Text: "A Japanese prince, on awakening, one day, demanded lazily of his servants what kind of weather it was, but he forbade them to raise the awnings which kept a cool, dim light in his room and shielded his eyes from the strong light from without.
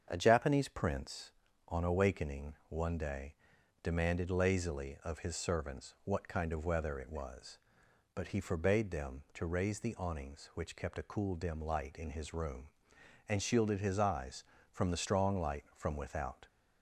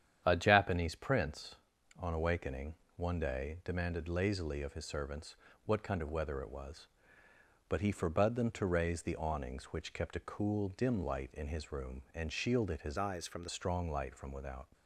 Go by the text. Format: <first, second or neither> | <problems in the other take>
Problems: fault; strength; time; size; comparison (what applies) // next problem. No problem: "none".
first | starts louder than the rest; strong; until 1.2 s; 9 dB; strong in the first // pauses between "servants" and "what"; slight; at 5.3 s; 0.30 s long // changes voice from "eyes" to "the"; from 12.9 to 13.4 s; 0.5 s long